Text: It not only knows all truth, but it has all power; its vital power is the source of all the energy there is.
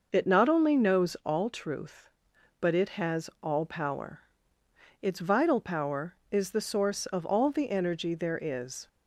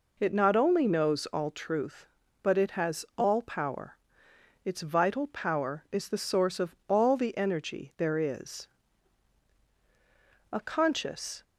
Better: first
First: none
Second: goes on to say "A conscious"; noticeable; from 10.5 s on; 0.90 s long

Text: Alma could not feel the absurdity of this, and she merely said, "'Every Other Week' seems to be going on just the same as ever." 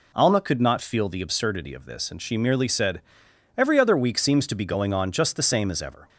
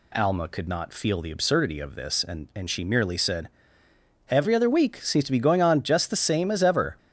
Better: first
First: none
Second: says "and" twice; at 2.5 s

